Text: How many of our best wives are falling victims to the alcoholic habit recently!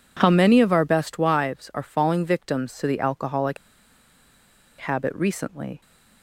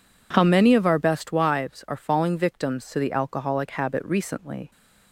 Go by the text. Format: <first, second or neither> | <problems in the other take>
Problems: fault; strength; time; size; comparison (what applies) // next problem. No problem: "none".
second | pauses between "alcoholic" and "habit"; at 3.5 s; 1.2 s long